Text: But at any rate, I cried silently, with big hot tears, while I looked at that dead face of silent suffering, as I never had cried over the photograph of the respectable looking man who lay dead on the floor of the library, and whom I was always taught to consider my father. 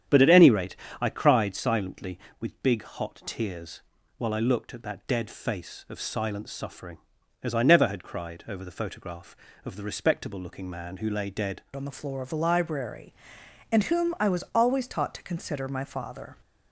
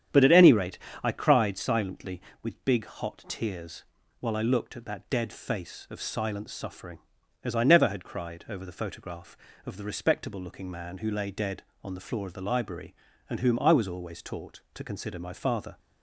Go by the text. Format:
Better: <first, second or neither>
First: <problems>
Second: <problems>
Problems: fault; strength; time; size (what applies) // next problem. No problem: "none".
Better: second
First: starts louder than the rest; strong; until 1.3 s; 9 dB // changes voice at "on"; from 11.7 s on; 4.6 s long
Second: starts louder than the rest; strong; until 1.3 s; 9 dB